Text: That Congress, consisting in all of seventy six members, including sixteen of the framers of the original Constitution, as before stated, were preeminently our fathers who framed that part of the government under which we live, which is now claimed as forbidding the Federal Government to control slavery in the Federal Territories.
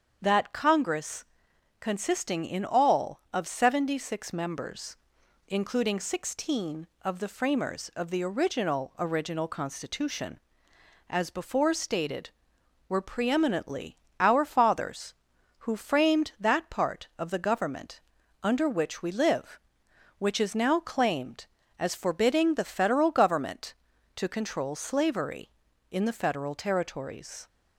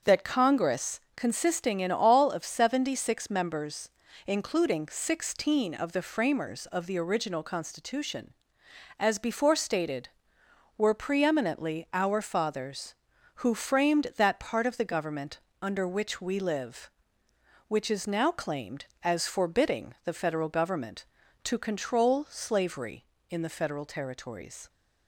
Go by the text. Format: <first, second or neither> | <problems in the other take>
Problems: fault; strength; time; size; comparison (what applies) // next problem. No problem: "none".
second | starts louder than the rest; strong; until 1.2 s; 7 dB; also in the second // says "original" twice; at 8.9 s // pauses between "preeminently" and "our"; slight; at 13.9 s; 0.20 s long // pauses between "government" and "under"; at 18.0 s; 0.42 s long; slight in the second